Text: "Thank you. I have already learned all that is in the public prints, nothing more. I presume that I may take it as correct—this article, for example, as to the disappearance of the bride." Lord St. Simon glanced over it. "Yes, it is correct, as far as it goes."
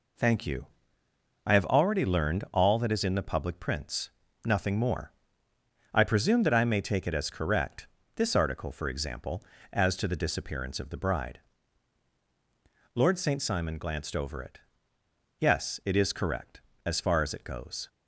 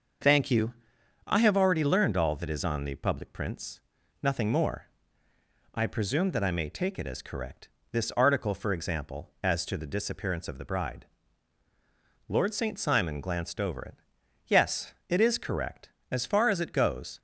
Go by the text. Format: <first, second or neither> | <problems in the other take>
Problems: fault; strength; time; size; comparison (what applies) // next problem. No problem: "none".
first | starts louder than the rest; noticeable; until 1.7 s; 6 dB // says "on" for "in"; at 2.6 s